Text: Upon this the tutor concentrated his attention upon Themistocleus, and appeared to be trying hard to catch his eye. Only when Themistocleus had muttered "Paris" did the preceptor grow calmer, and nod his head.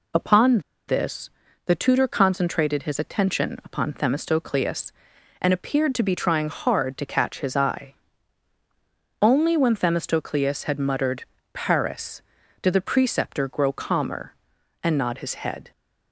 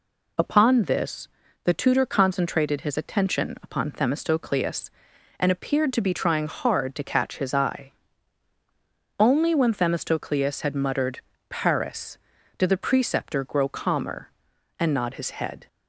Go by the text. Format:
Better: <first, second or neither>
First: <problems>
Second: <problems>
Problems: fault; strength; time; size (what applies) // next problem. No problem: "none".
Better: second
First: pauses between "Upon" and "this"; slight; at 0.5 s; 0.28 s long // pauses between "this" and "the"; slight; at 1.2 s; 0.36 s long // pauses between "muttered" and "Paris"; slight; at 11.2 s; 0.30 s long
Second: pauses between "this" and "the"; slight; at 1.2 s; 0.36 s long // pauses between "muttered" and "Paris"; slight; at 11.1 s; 0.30 s long